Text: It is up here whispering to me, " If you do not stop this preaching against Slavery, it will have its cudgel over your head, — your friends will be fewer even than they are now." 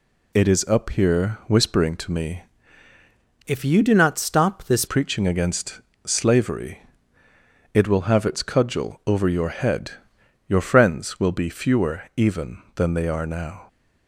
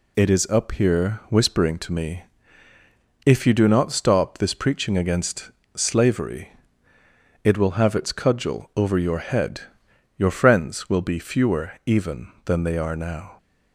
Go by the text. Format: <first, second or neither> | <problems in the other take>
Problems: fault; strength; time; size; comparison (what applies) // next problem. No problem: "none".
second | changes voice from "If" to "this"; from 3.4 to 4.8 s; 1.4 s long // pauses between "against" and "Slavery"; slight; at 5.7 s; 0.26 s long; slight in the second // pauses between "fewer" and "even"; slight; at 12.0 s; 0.16 s long; slight in the second